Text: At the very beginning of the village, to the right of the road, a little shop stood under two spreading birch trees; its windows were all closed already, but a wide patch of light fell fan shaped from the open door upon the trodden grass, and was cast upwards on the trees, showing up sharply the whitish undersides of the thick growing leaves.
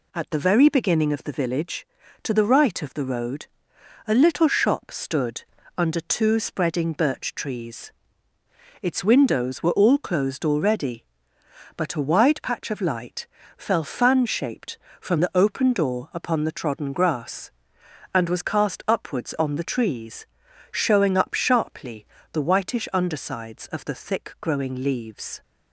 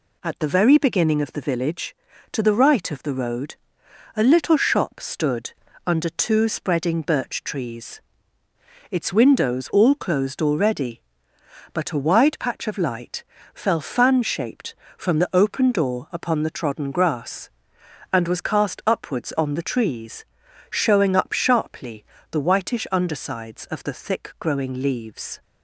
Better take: first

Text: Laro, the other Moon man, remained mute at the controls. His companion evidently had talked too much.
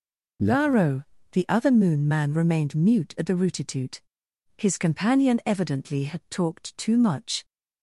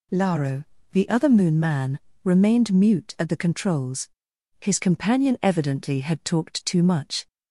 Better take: second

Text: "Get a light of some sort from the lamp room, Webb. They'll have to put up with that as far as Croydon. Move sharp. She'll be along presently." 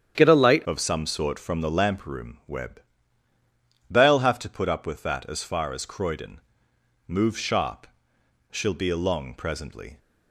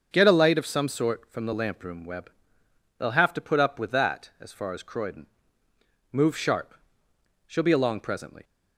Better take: second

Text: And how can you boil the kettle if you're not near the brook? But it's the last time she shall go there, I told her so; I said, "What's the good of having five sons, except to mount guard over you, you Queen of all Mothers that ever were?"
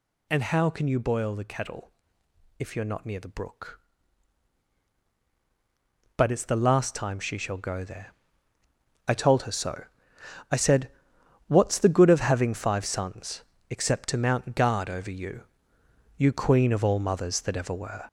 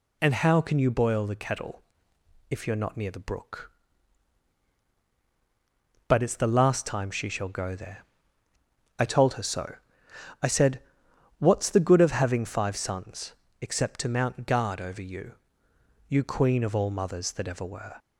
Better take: second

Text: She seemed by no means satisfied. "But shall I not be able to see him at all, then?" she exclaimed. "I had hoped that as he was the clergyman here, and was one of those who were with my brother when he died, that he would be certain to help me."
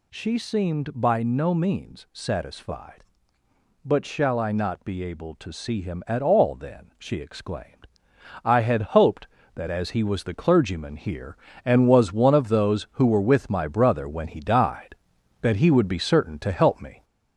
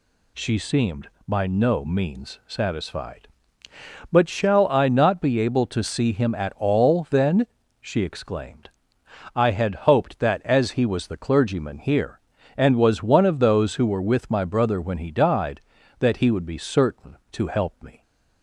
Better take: second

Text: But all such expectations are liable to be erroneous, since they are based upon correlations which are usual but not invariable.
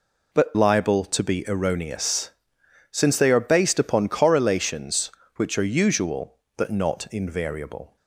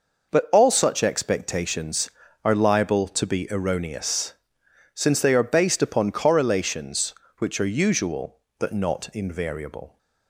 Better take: second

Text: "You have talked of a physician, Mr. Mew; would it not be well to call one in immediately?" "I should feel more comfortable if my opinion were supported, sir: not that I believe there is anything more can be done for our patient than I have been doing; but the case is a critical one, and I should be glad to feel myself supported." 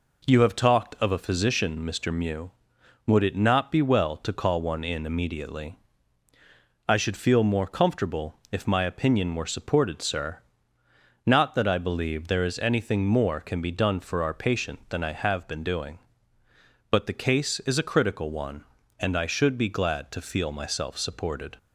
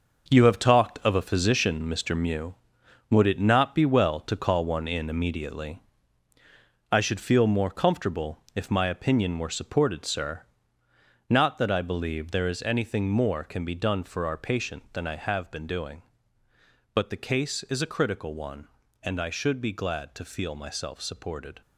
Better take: first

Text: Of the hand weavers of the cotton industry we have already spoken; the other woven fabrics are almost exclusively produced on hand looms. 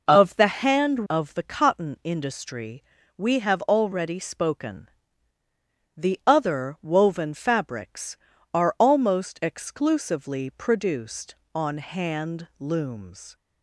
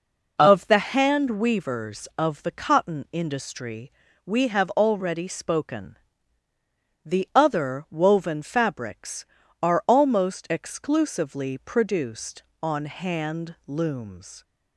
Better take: second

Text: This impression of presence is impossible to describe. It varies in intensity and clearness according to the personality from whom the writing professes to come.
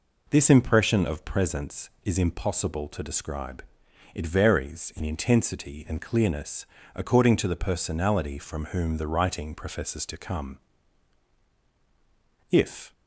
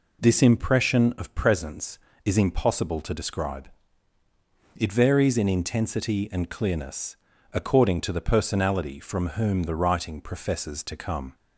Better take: second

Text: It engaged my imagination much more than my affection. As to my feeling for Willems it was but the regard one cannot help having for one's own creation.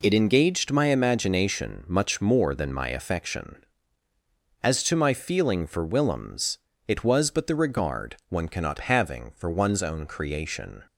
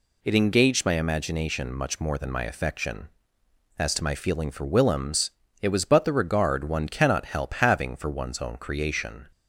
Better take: second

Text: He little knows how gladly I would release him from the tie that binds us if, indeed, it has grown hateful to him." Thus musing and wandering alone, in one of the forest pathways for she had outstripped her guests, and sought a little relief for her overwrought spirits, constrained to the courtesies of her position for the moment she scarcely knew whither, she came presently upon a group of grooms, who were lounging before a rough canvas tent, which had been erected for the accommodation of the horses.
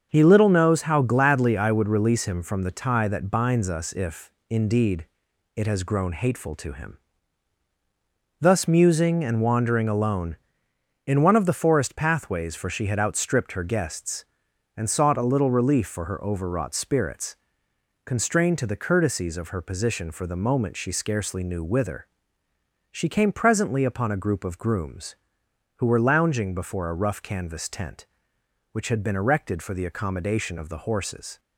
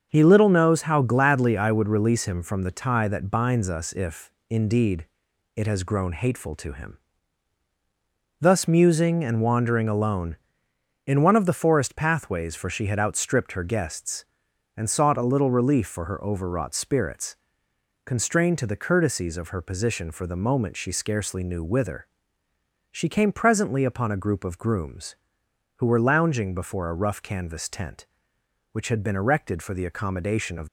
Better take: first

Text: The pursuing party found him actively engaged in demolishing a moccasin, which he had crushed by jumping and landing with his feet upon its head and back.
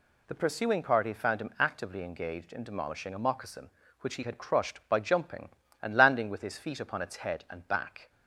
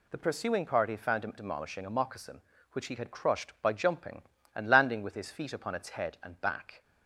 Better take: first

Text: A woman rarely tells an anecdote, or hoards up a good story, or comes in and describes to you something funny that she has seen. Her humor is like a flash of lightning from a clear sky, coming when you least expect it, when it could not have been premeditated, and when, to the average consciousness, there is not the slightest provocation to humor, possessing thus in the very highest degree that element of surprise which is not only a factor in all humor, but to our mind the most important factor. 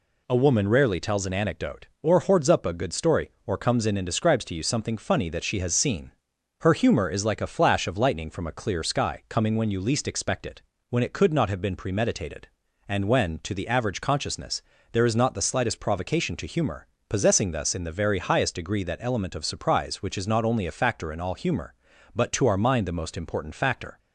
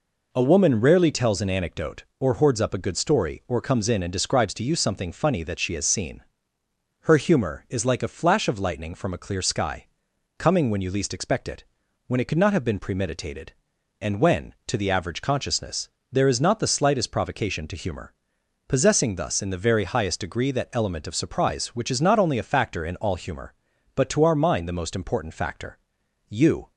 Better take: first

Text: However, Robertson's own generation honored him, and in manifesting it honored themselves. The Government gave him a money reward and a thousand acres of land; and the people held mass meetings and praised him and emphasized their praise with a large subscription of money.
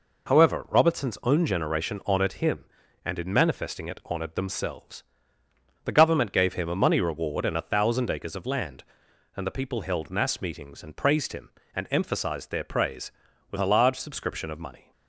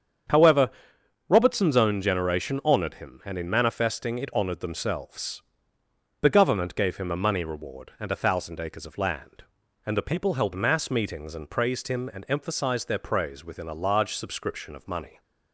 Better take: first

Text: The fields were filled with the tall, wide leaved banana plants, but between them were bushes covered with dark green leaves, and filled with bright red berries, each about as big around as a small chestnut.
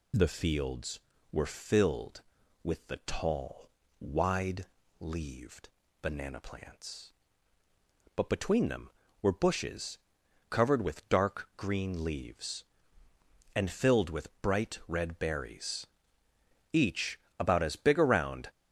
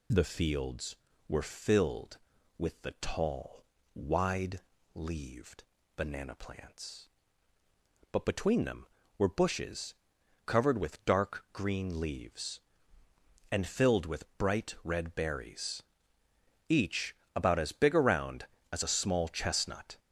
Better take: second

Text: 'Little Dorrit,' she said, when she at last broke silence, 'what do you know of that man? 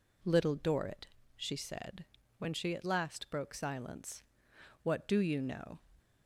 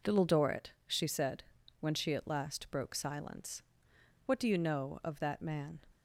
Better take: second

